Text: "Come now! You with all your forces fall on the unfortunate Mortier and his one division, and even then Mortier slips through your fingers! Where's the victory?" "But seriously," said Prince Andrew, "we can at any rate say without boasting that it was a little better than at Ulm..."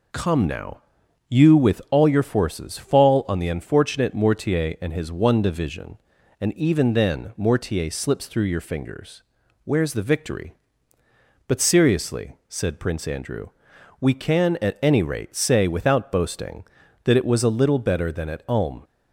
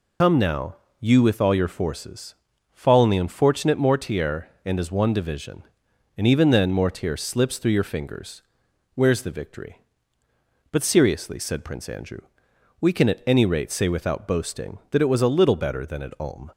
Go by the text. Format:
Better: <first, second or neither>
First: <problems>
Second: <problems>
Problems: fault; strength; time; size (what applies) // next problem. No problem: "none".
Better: first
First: none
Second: loses the start of "Come"; at 0.2 s; 85 ms // pauses between "forces" and "fall"; at 2.3 s; 0.40 s long